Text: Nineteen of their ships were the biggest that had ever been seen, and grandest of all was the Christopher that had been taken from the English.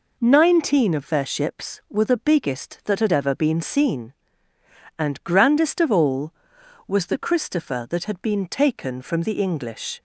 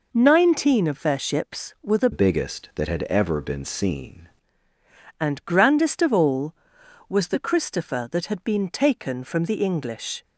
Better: first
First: none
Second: changes voice from "biggest" to "seen"; from 2.1 to 4.2 s; 2.1 s long

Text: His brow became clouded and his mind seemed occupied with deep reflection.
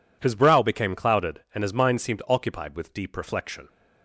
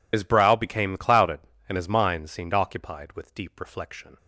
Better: first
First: none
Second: loses the start of "His"; at 0.1 s; 75 ms

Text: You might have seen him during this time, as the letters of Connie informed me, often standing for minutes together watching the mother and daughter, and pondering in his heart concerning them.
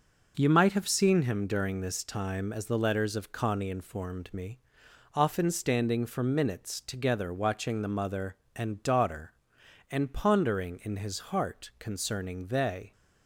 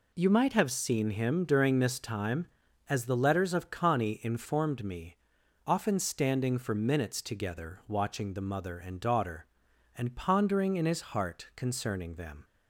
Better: second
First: says "they" for "them"; at 12.4 s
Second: none

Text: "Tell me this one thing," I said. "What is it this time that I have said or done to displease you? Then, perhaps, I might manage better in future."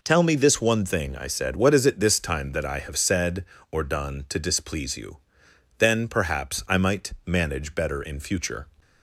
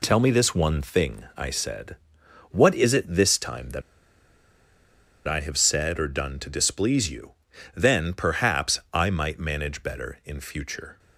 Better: first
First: none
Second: pauses between "that" and "I"; strong; at 3.8 s; 1.4 s long

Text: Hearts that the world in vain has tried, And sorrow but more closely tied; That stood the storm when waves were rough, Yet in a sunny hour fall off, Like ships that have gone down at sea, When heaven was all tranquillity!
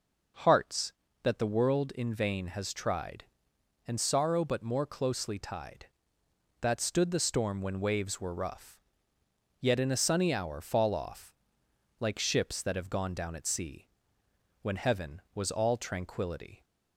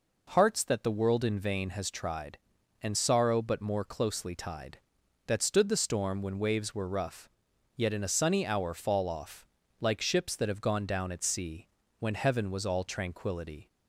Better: neither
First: none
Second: none

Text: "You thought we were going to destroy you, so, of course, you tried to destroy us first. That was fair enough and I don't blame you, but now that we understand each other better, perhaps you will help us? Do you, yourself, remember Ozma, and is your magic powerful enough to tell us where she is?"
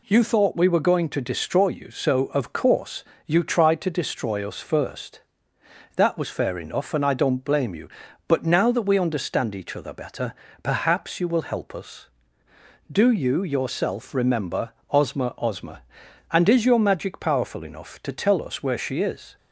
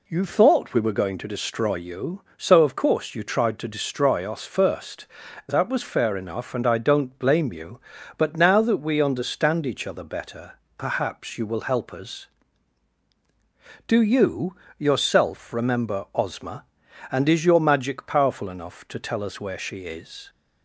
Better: second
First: pauses between "remember" and "Ozma"; slight; at 14.7 s; 0.20 s long // says "Ozma" twice; at 15.3 s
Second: none

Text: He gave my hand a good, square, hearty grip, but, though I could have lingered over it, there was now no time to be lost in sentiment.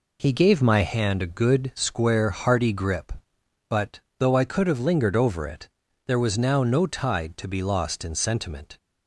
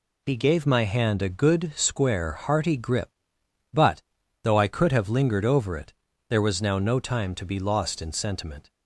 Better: second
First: says "tide" for "time"; at 6.8 s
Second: none

